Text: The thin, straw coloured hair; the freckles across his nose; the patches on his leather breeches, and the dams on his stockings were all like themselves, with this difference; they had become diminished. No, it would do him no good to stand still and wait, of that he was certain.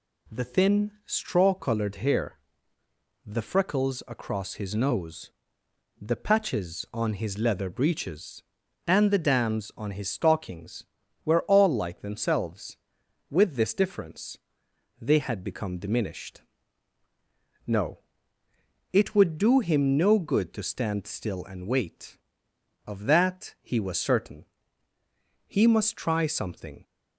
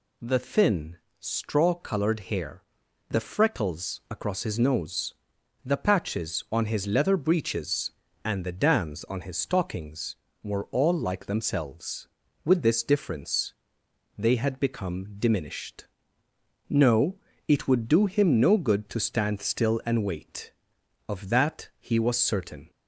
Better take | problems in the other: second | goes on to say "He must try something"; from 25.4 s on; 1.3 s long

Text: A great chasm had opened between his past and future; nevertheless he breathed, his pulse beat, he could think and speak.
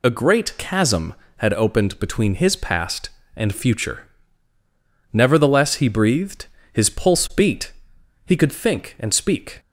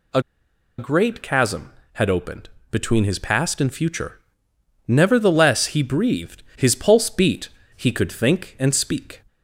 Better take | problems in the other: first | pauses between "A" and "great"; noticeable; at 0.1 s; 0.58 s long // pauses between "opened" and "between"; slight; at 2.4 s; 0.22 s long

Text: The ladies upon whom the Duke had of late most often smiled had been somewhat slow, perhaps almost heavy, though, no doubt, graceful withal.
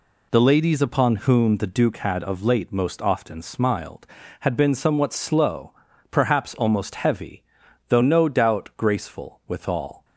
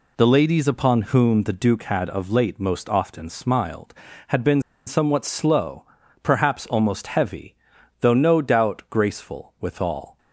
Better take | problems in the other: first | pauses between "been" and "somewhat"; slight; at 4.6 s; 0.25 s long

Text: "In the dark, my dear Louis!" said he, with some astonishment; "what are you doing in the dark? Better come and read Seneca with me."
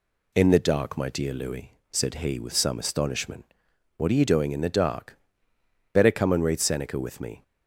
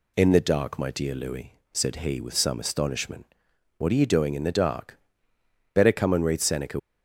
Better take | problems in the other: first | stops before "with me"; at 6.7 s

